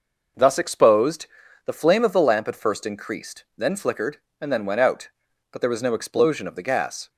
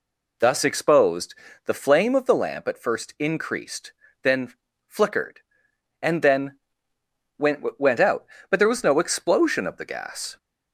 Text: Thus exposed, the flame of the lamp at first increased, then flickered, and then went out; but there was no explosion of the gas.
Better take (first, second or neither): first